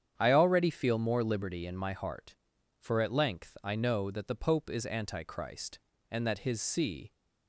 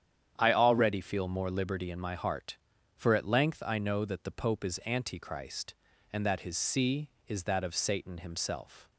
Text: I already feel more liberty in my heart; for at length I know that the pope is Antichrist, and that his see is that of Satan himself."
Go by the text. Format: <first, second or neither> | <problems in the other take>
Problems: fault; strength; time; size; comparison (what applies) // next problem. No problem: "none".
second | starts louder than the rest; strong; until 1.1 s; 8.5 dB; strong in the second // stops before "is that of Satan himself"; at 7.1 s